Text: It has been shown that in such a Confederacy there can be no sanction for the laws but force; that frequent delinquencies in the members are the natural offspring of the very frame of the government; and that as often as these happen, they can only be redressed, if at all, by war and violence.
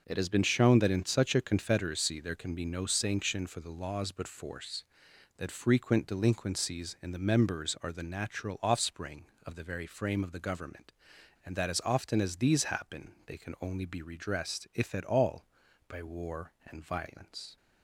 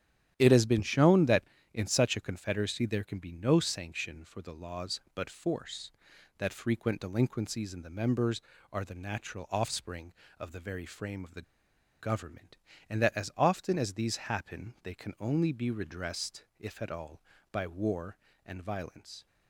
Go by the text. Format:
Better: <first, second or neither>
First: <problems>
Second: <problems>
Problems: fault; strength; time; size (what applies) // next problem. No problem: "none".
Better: first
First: none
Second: starts louder than the rest; strong; until 1.3 s; 11 dB // pauses between "the" and "government"; noticeable; at 11.4 s; 0.57 s long